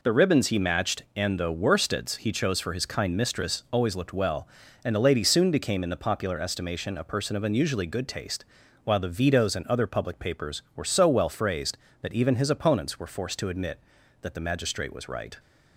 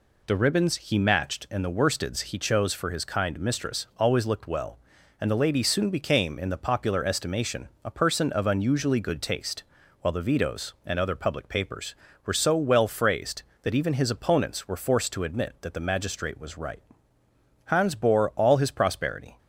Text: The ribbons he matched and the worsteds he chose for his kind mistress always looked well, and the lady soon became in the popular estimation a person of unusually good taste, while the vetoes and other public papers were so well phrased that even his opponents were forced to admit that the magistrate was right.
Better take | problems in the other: first | pauses between "estimation" and "a"; slight; at 7.6 s; 0.16 s long // goes on to say "Hans bore all his prosperity"; strong; from 17.6 s on; 1.7 s long

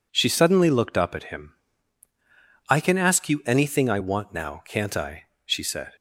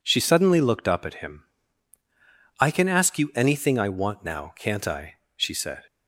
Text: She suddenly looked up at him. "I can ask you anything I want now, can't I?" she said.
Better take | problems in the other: neither | none

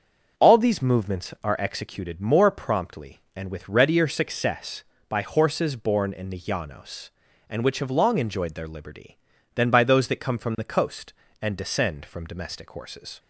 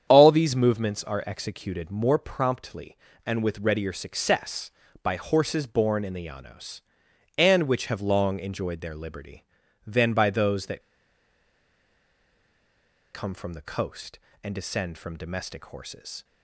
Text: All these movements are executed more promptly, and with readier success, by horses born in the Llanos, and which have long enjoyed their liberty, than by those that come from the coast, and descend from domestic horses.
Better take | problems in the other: first | starts louder than the rest; strong; until 1.1 s; 8.5 dB; also in the first // pauses between "that" and "come"; strong; at 10.8 s; 2.3 s long

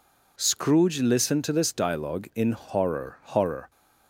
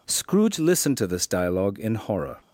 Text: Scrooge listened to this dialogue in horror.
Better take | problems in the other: second | says "horror" twice; at 3.2 s

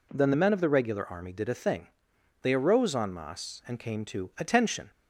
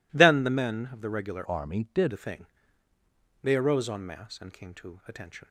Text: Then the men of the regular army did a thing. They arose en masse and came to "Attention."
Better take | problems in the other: first | changes voice from "army" to "did"; from 1.4 to 2.1 s; 0.7 s long

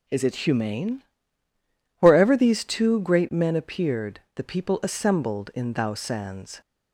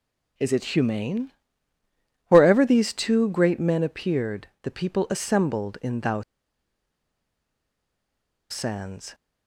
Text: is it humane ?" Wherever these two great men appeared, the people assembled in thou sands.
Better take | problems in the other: first | pauses between "thou" and "sands"; strong; at 6.2 s; 2.2 s long

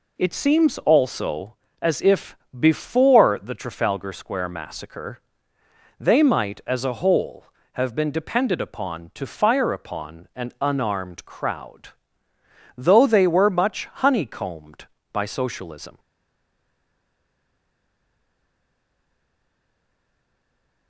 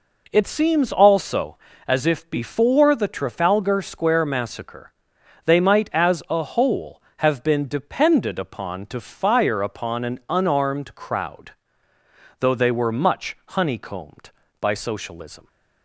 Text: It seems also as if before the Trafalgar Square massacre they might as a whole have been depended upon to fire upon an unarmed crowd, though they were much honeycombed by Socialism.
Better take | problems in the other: second | pauses between "if" and "before"; slight; at 2.3 s; 0.22 s long // pauses between "massacre" and "they"; noticeable; at 5.1 s; 0.80 s long; noticeable in the second // stays silent after the last word; strong; from 15.9 s on; 4.9 s long

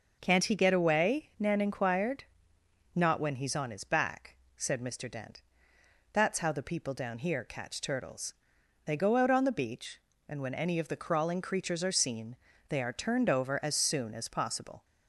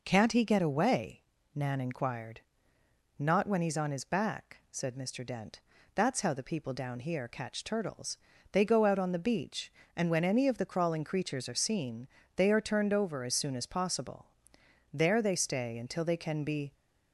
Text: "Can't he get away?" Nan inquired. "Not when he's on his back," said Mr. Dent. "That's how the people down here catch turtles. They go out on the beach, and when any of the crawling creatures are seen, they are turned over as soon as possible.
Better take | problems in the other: first | goes on to say "There they stay until they can be"; strong; from 14.9 s on; 1.8 s long

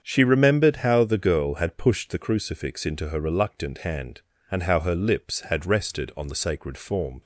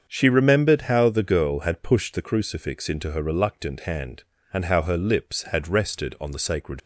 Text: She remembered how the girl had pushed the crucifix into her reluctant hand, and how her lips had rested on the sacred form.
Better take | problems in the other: first | starts louder than the rest; strong; until 1.1 s; 7 dB; strong in the first // stops before "form"; at 6.8 s

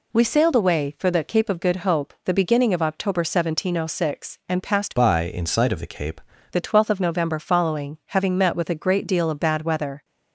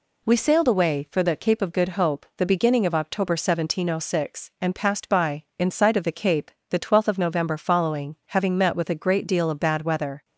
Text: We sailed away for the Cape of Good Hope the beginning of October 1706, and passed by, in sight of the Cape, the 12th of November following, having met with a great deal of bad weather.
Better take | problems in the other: second | changes voice from "by" to "Cape"; from 4.9 to 6.2 s; 1.3 s long

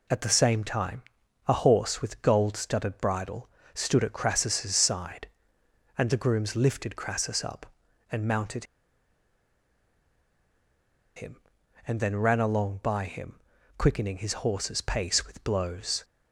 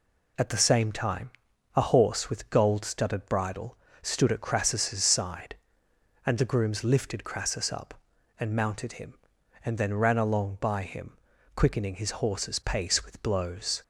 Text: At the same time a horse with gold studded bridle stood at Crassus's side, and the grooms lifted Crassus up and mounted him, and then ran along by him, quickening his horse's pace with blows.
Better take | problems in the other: second | pauses between "time" and "a"; noticeable; at 1.0 s; 0.46 s long; noticeable in the second // pauses between "bridle" and "stood"; slight; at 3.4 s; 0.26 s long; slight in the second // pauses between "mounted" and "him"; strong; at 8.6 s; 2.5 s long

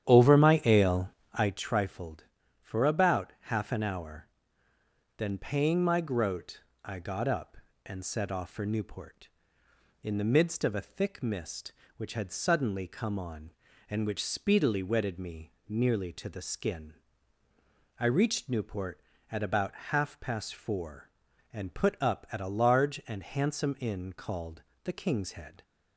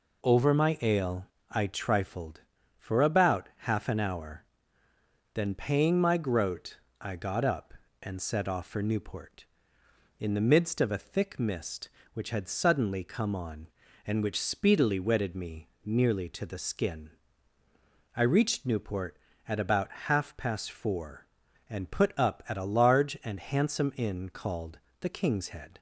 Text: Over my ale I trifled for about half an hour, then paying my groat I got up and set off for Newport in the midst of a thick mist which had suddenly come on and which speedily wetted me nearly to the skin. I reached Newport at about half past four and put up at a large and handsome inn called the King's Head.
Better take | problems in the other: second | starts louder than the rest; strong; until 1.6 s; 10 dB // pauses between "ale" and "I"; slight; at 1.0 s; 0.24 s long; slight in the second // pauses between "groat" and "I"; slight; at 6.6 s; 0.24 s long; slight in the second // pauses between "about" and "half"; slight; at 19.7 s; 0.16 s long; slight in the second // pauses between "called" and "the"; slight; at 24.6 s; 0.22 s long; slight in the second

